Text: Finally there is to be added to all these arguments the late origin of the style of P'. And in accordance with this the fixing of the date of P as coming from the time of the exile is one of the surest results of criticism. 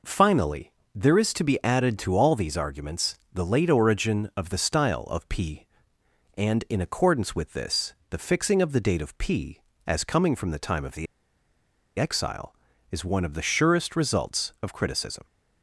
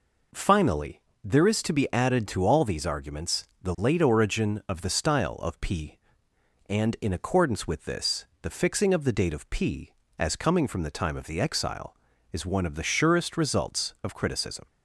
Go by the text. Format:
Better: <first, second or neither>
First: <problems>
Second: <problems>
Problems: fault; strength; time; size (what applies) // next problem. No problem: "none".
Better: second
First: pauses between "Finally" and "there"; slight; at 0.7 s; 0.22 s long // pauses between "this" and "the"; slight; at 7.9 s; 0.16 s long // pauses between "the" and "exile"; noticeable; at 11.0 s; 0.93 s long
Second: pauses between "Finally" and "there"; slight; at 1.0 s; 0.22 s long // pauses between "this" and "the"; slight; at 8.2 s; 0.16 s long